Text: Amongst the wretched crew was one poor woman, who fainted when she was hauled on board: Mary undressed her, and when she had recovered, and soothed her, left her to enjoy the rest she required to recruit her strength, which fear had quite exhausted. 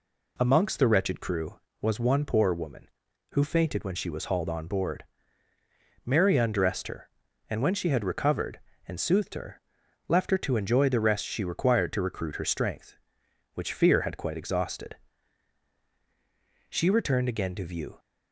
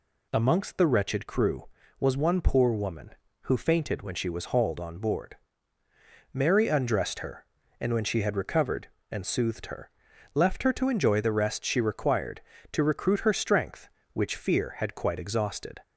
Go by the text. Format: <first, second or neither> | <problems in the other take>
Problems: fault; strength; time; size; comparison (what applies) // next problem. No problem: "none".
second | goes on to say "She returned again to view"; noticeable; from 16.6 s on; 1.3 s long